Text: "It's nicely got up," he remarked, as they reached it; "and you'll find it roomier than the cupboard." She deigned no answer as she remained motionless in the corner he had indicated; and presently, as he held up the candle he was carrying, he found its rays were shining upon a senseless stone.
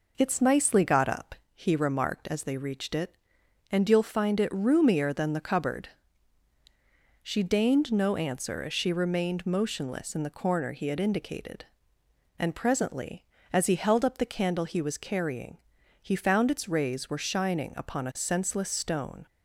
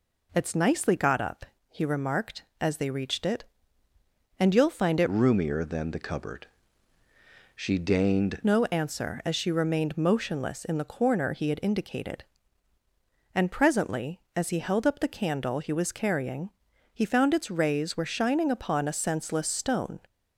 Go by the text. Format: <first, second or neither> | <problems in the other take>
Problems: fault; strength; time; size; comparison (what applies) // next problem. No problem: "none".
first | changes voice from "roomier" to "deigned"; from 5.0 to 8.4 s; 3.4 s long